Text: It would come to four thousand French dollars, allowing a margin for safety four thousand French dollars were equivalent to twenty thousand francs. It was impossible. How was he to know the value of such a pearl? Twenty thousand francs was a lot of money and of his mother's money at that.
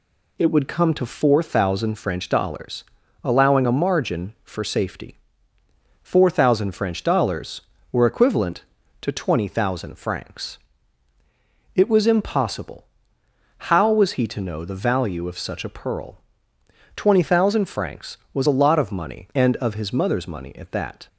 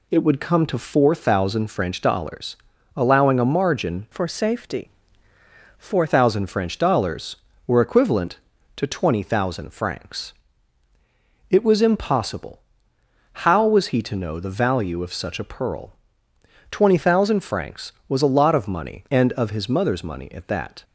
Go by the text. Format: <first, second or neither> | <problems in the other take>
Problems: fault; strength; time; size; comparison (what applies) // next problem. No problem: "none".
first | changes voice from "for" to "four"; from 4.1 to 6.0 s; 1.9 s long // pauses between "safety" and "four"; noticeable; at 4.9 s; 0.88 s long; noticeable in the first